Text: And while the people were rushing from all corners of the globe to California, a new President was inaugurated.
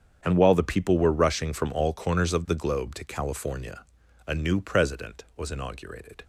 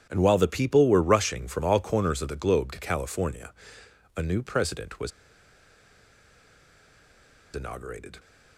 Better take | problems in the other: first | starts louder than the rest; strong; until 1.1 s; 9.5 dB; strong in the first // pauses between "was" and "inaugurated"; strong; at 5.1 s; 2.4 s long

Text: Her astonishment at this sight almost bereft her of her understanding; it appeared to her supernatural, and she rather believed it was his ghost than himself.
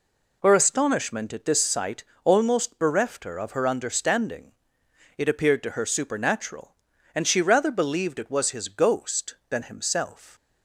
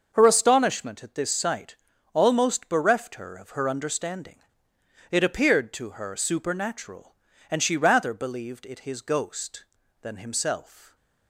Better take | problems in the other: first | starts louder than the rest; until 1.1 s; 6 dB // pauses between "sight" and "almost"; at 1.7 s; 0.38 s long; slight in the first // skips "was"; at 8.8 s

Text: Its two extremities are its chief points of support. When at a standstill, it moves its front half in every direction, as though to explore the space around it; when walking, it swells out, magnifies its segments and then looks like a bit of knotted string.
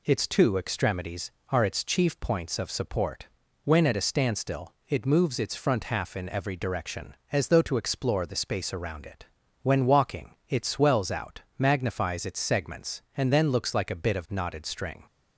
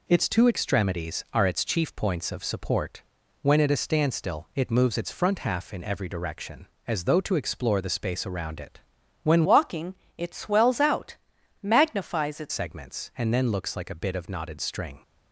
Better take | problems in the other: first | changes voice from "walking" to "its"; from 9.4 to 12.5 s; 3.1 s long

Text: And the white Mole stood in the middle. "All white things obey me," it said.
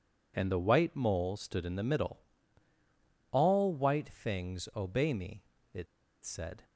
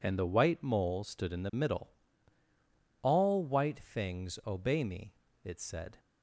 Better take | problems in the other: second | pauses between "it" and "said"; at 5.8 s; 0.38 s long

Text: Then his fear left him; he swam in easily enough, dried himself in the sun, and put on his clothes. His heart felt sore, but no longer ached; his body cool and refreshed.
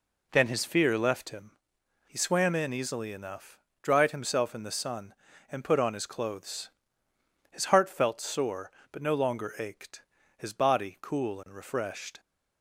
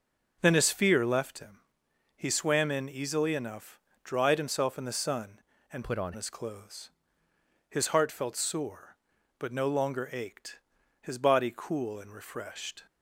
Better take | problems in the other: first | changes voice from "put" to "on"; from 5.8 to 6.1 s; 0.3 s long

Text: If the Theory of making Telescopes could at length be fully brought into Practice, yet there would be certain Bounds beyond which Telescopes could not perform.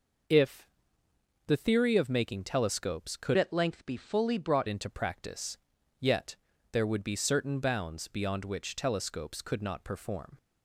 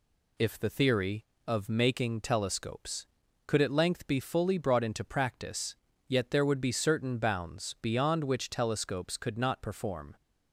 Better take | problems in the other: second | pauses between "If" and "the"; noticeable; at 0.6 s; 0.80 s long // changes voice from "at" to "brought"; from 3.3 to 4.6 s; 1.3 s long // pauses between "yet" and "there"; at 6.3 s; 0.38 s long

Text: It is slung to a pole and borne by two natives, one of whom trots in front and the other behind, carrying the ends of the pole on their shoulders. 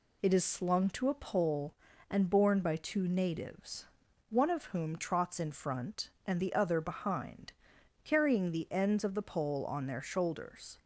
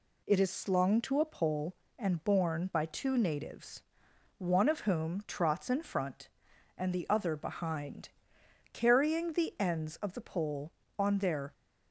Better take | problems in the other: first | stops before "shoulders"; at 11.5 s

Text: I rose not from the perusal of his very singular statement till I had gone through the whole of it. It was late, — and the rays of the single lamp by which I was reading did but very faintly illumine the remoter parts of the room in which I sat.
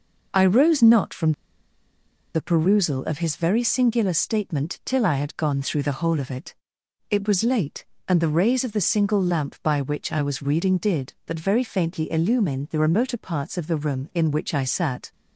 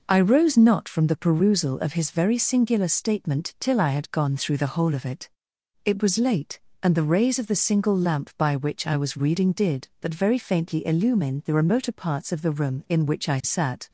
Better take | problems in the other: second | pauses between "from" and "the"; at 1.3 s; 1.0 s long

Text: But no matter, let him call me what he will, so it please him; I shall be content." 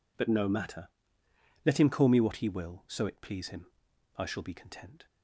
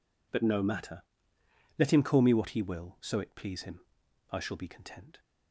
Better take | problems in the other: neither | none

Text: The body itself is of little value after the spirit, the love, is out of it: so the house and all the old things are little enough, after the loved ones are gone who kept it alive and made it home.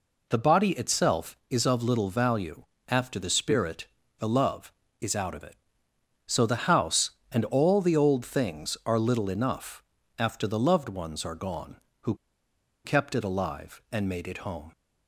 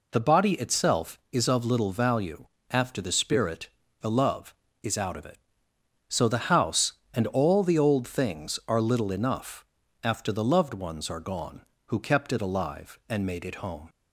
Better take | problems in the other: second | pauses between "value" and "after"; slight; at 2.6 s; 0.24 s long; slight in the second // pauses between "who" and "kept"; noticeable; at 12.1 s; 0.70 s long

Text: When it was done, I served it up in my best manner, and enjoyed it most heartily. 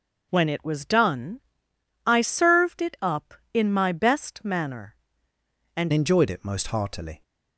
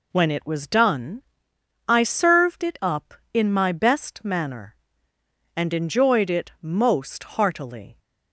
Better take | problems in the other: second | changes voice at "enjoyed"; from 5.9 s on; 1.3 s long

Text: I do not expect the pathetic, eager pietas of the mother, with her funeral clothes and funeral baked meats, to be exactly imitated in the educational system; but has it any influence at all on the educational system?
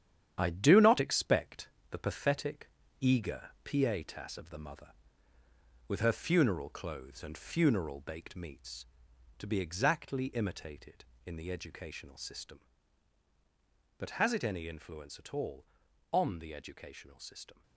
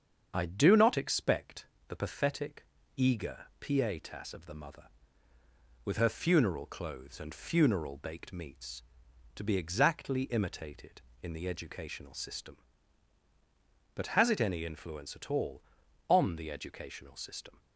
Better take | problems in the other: second | gets quieter; strong; throughout; 8 dB // starts louder than the rest; strong; until 1.4 s; 9.5 dB; also in the second // pauses between "expect" and "the"; slight; at 1.6 s; 0.20 s long; slight in the second // pauses between "eager" and "pietas"; slight; at 3.4 s; 0.16 s long; slight in the second

